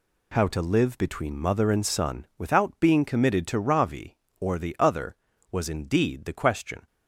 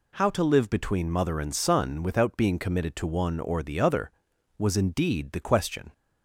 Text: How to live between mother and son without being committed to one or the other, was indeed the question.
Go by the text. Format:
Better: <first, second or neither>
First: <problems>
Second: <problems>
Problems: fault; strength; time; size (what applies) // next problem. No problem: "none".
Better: second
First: says "ravi" for "one"; at 3.5 s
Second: none